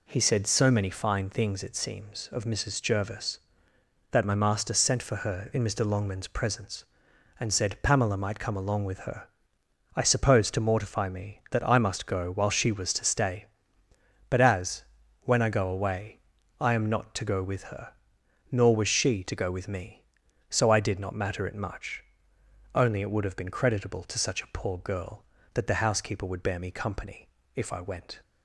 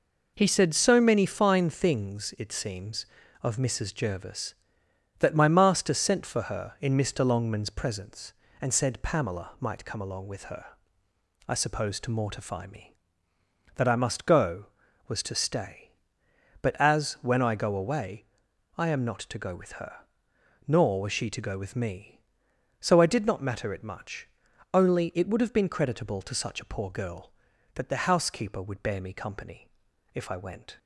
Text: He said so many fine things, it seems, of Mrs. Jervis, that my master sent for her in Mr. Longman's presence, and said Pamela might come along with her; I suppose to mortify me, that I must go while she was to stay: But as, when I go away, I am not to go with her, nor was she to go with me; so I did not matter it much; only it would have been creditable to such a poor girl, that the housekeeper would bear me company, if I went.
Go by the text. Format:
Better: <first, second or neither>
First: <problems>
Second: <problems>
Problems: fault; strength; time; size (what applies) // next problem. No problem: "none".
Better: first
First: none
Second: skips "while she"; at 14.8 s